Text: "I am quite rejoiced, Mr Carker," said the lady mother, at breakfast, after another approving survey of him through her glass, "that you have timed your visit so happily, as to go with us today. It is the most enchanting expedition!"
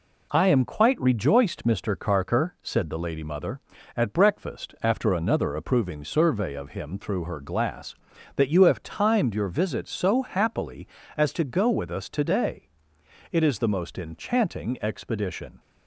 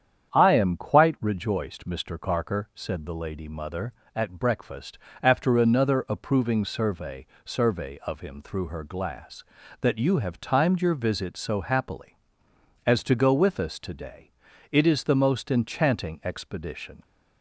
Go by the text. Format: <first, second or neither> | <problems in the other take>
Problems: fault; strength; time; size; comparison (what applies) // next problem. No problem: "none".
first | starts louder than the rest; strong; until 1.3 s; 8.5 dB // says "survey" twice; at 7.4 s